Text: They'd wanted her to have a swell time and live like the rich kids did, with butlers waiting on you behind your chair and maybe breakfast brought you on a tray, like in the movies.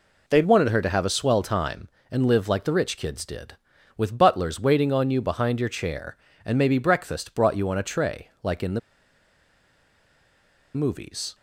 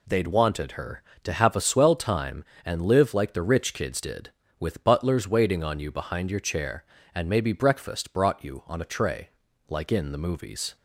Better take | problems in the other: second | pauses between "the" and "movies"; strong; at 8.7 s; 1.9 s long

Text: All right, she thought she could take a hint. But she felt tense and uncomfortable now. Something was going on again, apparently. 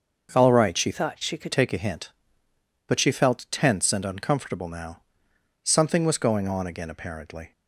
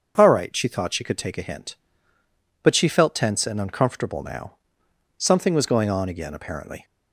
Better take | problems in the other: second | starts louder than the rest; until 1.3 s; 6 dB; also in the second // changes voice from "thought" to "could"; from 0.9 to 1.5 s; 0.6 s long

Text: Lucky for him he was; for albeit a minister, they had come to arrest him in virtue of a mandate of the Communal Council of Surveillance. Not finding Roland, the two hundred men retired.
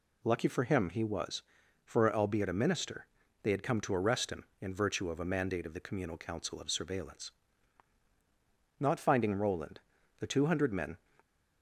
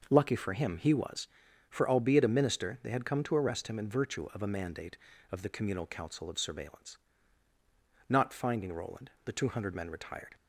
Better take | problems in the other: second | stops before "retired"; at 11.1 s

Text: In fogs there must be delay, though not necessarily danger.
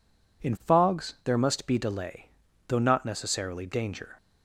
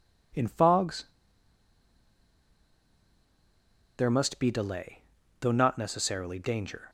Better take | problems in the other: first | pauses between "fogs" and "there"; strong; at 1.0 s; 2.9 s long

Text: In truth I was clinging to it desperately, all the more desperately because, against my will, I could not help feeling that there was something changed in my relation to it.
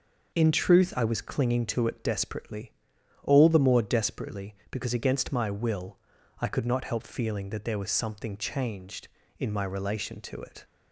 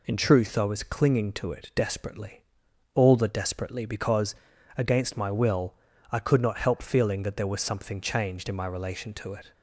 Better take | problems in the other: first | skips "more"; at 3.2 s

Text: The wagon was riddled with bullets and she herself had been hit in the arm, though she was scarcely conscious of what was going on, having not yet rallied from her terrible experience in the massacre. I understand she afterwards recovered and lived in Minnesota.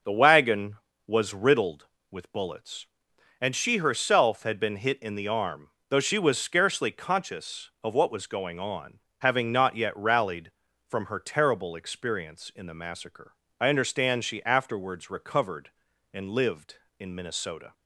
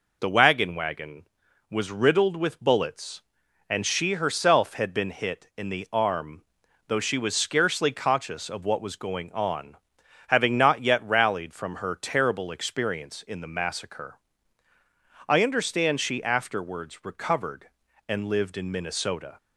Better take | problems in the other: first | says "wagon" twice; at 0.7 s

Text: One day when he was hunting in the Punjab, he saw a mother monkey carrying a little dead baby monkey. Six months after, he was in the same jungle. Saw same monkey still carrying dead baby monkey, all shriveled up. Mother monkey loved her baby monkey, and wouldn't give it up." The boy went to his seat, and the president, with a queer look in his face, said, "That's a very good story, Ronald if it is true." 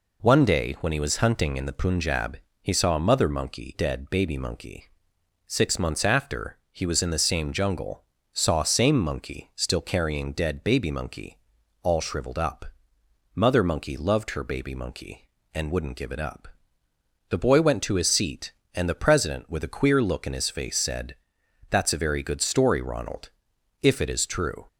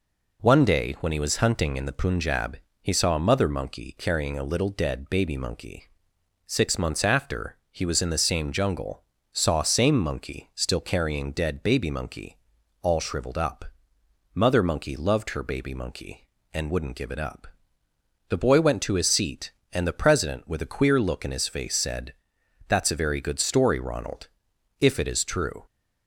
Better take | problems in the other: second | skips "carrying a little"; at 3.7 s // pauses between "Ronald" and "if"; noticeable; at 23.2 s; 0.52 s long; noticeable in the second

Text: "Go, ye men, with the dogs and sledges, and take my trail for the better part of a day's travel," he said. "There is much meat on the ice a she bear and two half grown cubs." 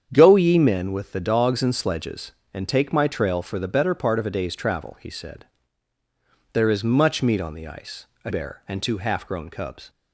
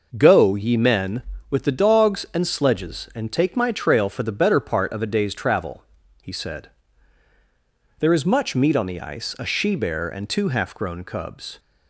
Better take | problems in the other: second | starts louder than the rest; strong; until 1.1 s; 8 dB // pauses between "ice" and "a"; slight; at 8.0 s; 0.18 s long // skips "she"; at 8.3 s

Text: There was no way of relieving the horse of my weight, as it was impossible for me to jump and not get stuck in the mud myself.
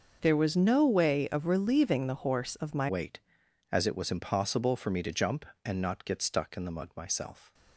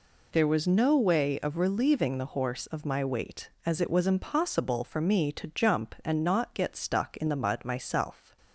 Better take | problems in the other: second | changes voice at "weight"; from 2.8 s on; 4.7 s long

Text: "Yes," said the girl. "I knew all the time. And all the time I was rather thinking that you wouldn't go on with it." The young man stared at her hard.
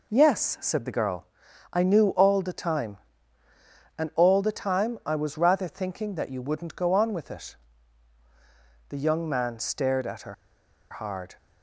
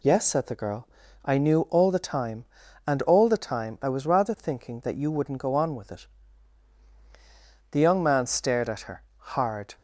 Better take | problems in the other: second | pauses between "her" and "hard"; noticeable; at 10.3 s; 0.56 s long

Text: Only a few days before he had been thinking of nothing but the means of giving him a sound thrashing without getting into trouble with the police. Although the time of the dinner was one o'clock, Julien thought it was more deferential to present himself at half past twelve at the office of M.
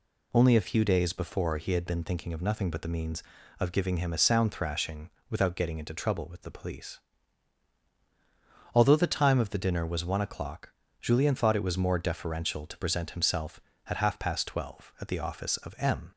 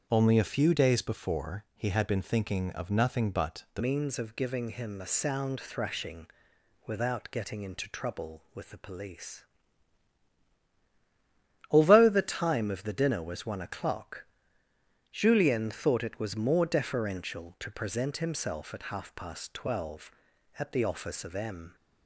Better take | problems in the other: first | starts louder than the rest; until 1.1 s; 7 dB // changes voice at "means"; from 3.8 s on; 17.9 s long // pauses between "thrashing" and "without"; noticeable; at 6.2 s; 0.58 s long; slight in the first

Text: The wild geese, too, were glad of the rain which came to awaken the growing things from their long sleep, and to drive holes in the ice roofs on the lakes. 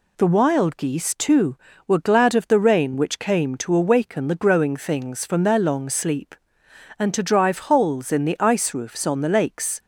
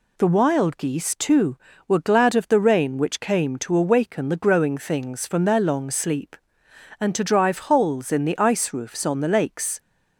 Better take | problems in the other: neither | none

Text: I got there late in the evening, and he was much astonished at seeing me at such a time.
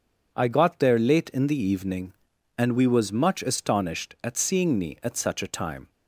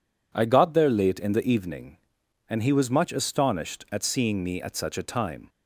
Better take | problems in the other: second | says "we" for "he"; at 2.7 s

